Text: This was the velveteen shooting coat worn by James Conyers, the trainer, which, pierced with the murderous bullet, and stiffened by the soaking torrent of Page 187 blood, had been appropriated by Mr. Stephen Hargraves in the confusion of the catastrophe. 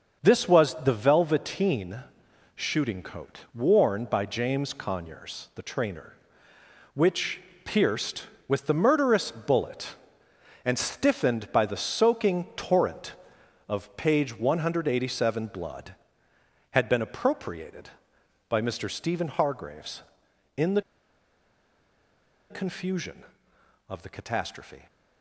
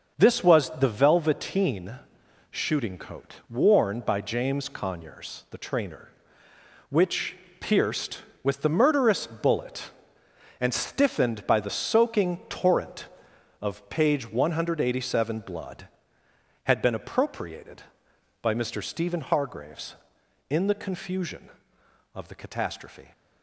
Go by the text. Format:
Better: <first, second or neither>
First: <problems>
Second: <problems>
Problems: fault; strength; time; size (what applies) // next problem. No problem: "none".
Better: second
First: starts louder than the rest; until 1.2 s; 6.5 dB // pauses between "velveteen" and "shooting"; noticeable; at 2.0 s; 0.56 s long // pauses between "the" and "confusion"; strong; at 20.8 s; 1.6 s long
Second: starts louder than the rest; until 1.2 s; 6.5 dB // pauses between "velveteen" and "shooting"; noticeable; at 1.9 s; 0.56 s long